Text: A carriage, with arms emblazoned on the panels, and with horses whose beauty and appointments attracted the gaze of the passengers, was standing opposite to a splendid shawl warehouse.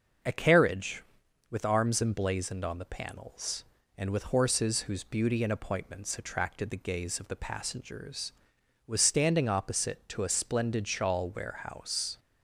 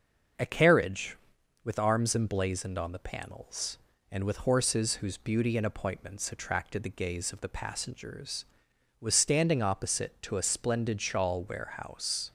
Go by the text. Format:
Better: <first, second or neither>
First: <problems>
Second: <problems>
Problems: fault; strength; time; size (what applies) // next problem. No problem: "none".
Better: neither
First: starts louder than the rest; noticeable; until 1.7 s; 6 dB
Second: starts louder than the rest; noticeable; until 1.8 s; 6 dB